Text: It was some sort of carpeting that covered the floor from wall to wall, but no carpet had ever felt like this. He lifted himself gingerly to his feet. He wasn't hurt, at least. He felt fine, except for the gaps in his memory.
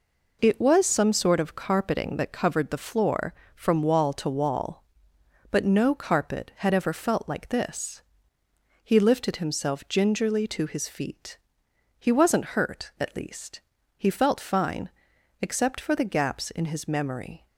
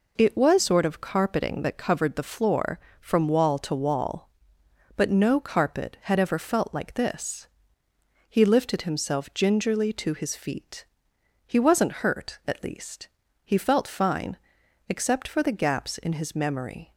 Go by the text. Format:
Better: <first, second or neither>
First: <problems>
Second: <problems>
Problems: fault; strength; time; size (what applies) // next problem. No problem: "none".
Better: first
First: none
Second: skips "some"; at 0.5 s